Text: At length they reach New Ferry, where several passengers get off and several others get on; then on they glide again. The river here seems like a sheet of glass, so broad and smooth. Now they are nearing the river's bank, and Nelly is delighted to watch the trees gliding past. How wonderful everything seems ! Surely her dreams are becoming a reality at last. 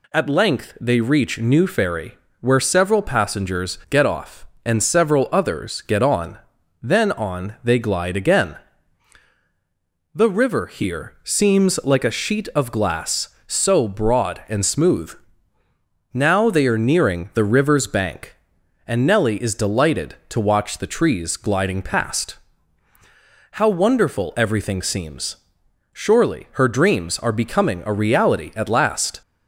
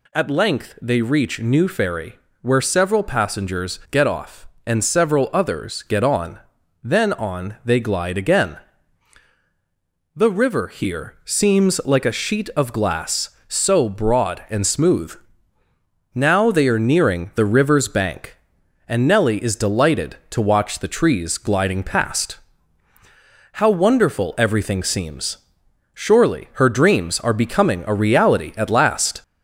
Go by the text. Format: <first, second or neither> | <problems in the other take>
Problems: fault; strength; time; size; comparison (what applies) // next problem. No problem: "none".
first | gets louder; slight; throughout; 2.5 dB